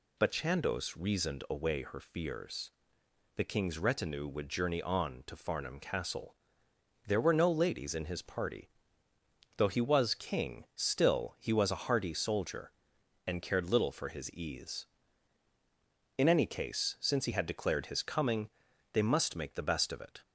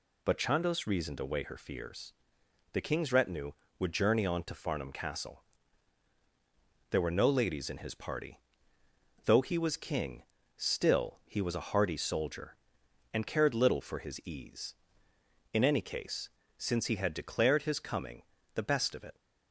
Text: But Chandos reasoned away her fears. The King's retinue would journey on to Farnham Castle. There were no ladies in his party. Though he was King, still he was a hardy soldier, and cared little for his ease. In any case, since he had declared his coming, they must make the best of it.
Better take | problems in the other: first | skips "they must make"; at 18.3 s

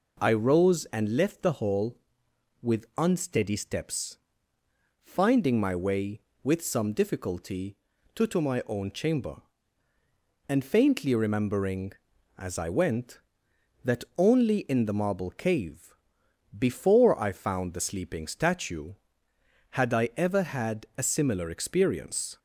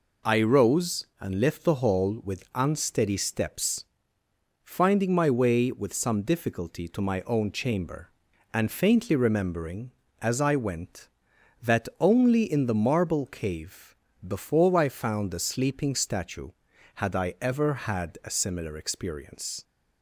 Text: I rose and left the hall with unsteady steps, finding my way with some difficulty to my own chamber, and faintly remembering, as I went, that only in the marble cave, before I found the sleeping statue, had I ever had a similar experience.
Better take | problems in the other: second | says "to" twice; at 8.2 s

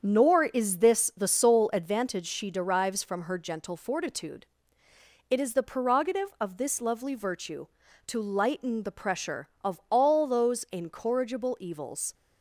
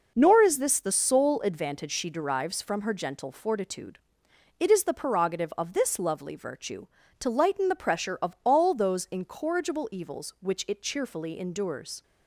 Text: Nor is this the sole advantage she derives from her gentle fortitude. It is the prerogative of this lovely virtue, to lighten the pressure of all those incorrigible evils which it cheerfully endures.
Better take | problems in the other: second | starts louder than the rest; strong; until 1.0 s; 7 dB // stops before "which it cheerfully endures"; at 12.1 s

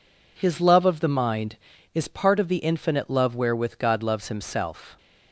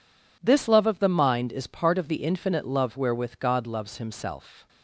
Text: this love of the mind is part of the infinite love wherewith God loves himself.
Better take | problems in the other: second | says "his" for "this"; at 0.3 s

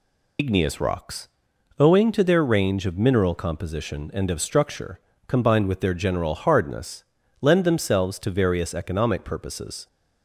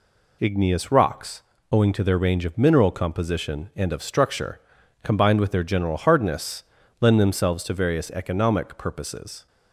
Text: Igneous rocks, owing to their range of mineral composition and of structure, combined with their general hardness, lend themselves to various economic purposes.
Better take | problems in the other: second | loses the start of "Igneous"; at 0.3 s; 65 ms

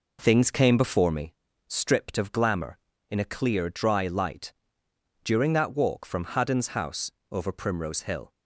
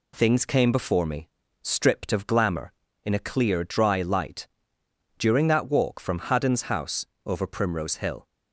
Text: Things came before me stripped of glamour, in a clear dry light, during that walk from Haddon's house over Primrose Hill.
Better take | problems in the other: second | starts louder than the rest; noticeable; until 1.3 s; 4 dB // pauses between "me" and "stripped"; slight; at 1.3 s; 0.34 s long; slight in the second // pauses between "house" and "over"; slight; at 7.1 s; 0.20 s long; slight in the second

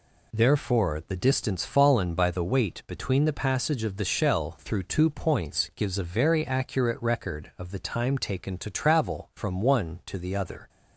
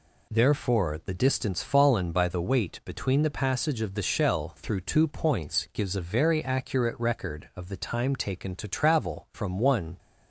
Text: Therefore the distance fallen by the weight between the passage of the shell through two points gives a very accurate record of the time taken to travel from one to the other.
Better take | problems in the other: first | stops before "to the other"; at 9.9 s

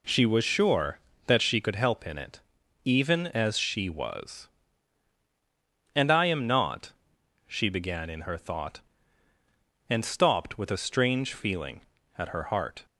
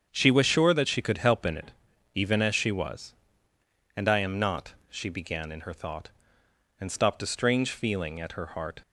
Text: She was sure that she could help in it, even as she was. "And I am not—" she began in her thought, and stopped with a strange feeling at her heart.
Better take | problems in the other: first | starts louder than the rest; strong; until 1.1 s; 7.5 dB // skips "with"; at 7.2 s

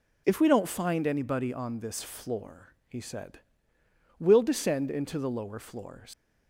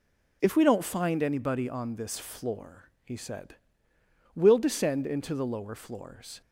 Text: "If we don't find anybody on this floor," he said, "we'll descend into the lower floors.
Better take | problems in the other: second | leaves "floors" unfinished; at 6.1 s; 110 ms

